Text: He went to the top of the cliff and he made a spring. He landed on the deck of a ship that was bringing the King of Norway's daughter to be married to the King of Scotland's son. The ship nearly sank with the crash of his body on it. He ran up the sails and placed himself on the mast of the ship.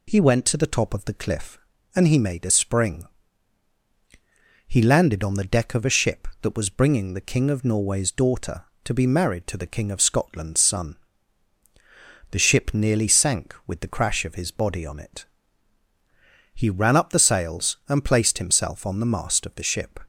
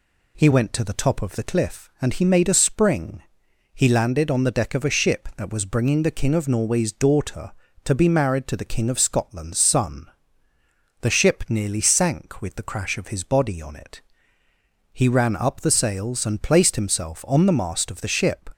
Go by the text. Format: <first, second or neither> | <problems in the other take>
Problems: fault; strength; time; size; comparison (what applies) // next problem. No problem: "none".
neither | none